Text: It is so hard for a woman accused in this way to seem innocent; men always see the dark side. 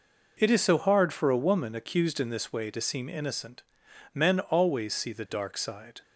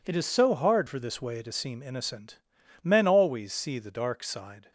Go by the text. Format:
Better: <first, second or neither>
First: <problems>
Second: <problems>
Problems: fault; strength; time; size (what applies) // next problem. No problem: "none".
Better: first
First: none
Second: skips "a woman accused in"; at 0.9 s